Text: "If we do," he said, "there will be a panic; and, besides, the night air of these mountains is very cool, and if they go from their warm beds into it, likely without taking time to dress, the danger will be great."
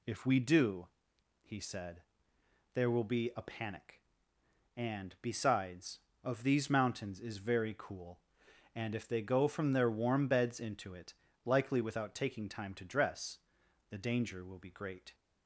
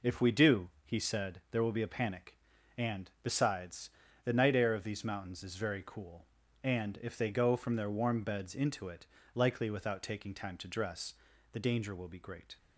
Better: second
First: skips "the night air"; at 6.1 s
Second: none

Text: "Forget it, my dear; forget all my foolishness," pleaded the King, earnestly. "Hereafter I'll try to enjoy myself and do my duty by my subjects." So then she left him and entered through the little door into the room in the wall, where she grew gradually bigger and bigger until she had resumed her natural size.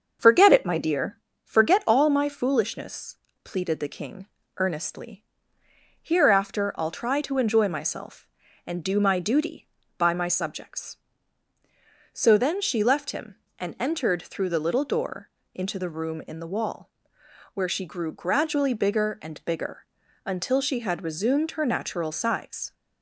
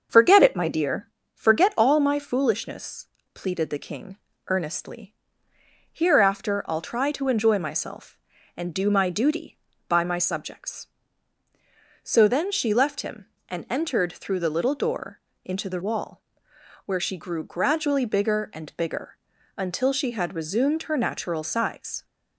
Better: first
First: starts louder than the rest; until 1.4 s; 6.5 dB // pauses between "door" and "into"; slight; at 15.3 s; 0.24 s long // pauses between "bigger" and "until"; at 19.8 s; 0.40 s long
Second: starts louder than the rest; until 1.3 s; 6.5 dB // pauses between "door" and "into"; slight; at 15.2 s; 0.24 s long // skips "room in the"; at 15.8 s // pauses between "bigger" and "until"; at 19.1 s; 0.40 s long

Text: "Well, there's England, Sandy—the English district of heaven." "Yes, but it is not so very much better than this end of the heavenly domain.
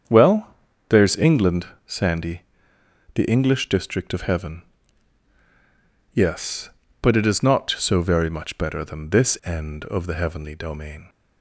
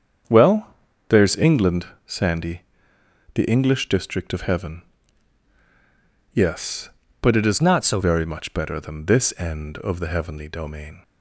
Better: first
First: starts louder than the rest; strong; until 1.4 s; 7.5 dB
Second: starts louder than the rest; strong; until 1.6 s; 7.5 dB // changes voice from "not" to "so"; from 7.6 to 8.0 s; 0.4 s long

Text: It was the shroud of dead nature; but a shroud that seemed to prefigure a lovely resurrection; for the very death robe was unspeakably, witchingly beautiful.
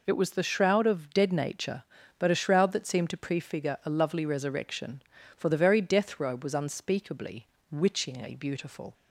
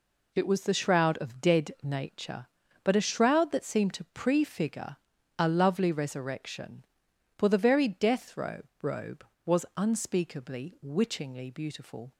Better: first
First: none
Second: pauses between "prefigure" and "a"; at 4.9 s; 0.44 s long // says "robe" twice; at 8.7 s

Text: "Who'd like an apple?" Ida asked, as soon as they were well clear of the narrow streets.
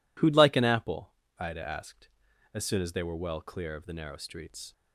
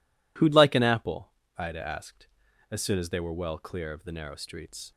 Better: neither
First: none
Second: none

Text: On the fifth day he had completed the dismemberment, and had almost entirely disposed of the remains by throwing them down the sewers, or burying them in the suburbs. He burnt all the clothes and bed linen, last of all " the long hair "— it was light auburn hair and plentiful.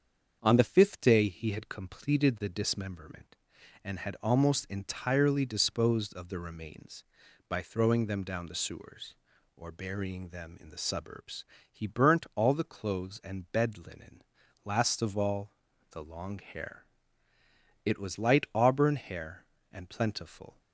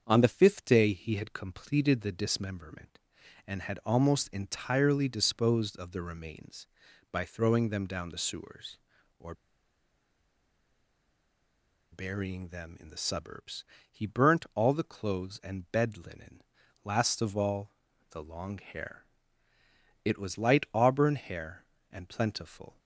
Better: first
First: starts louder than the rest; until 1.4 s; 7 dB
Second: starts louder than the rest; until 1.0 s; 7 dB // pauses between "or" and "burying"; strong; at 9.3 s; 2.5 s long

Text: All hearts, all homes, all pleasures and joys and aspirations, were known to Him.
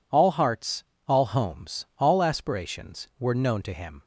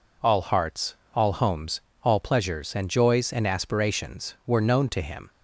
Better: second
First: skips "pleasures and joys and"; at 2.2 s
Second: none

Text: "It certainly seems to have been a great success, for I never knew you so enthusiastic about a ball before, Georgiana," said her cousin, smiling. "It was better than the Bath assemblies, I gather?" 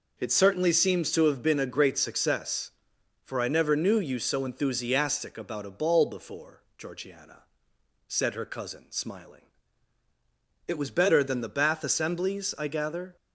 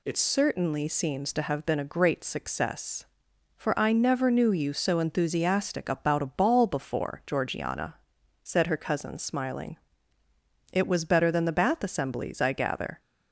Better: first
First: none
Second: changes voice at "certainly"; from 0.1 s on; 12.8 s long

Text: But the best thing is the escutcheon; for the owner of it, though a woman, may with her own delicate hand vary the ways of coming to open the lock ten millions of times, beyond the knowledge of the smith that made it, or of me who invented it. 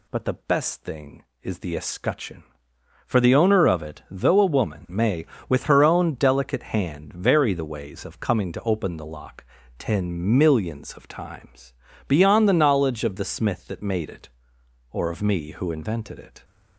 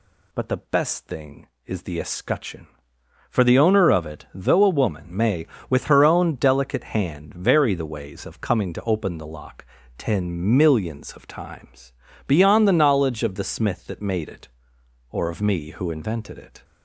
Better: neither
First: pauses between "lock" and "ten"; slight; at 9.4 s; 0.34 s long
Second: pauses between "lock" and "ten"; slight; at 9.6 s; 0.32 s long

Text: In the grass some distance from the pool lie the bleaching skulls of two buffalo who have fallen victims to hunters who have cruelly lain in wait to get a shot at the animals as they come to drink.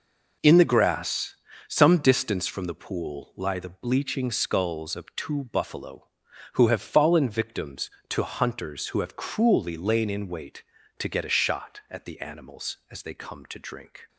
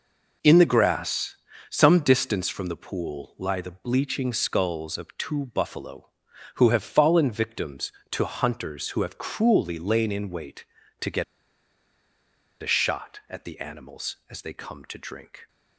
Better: first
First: pauses between "grass" and "some"; slight; at 1.3 s; 0.33 s long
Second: pauses between "grass" and "some"; slight; at 1.3 s; 0.34 s long // pauses between "get" and "a"; strong; at 11.2 s; 1.3 s long

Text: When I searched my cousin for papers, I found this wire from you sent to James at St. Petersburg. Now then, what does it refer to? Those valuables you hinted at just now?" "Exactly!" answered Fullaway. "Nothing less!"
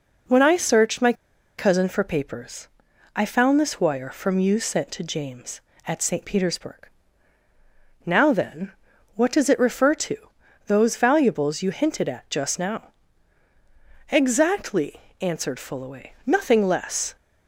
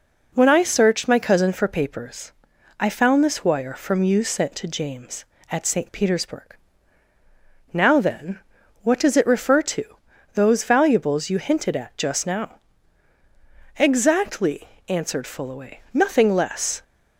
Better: second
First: pauses between "my" and "cousin"; at 1.1 s; 0.45 s long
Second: none

